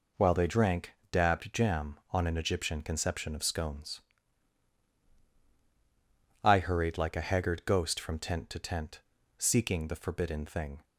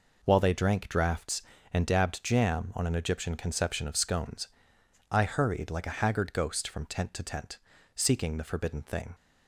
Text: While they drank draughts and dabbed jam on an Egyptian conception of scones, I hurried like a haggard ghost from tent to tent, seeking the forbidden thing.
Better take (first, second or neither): second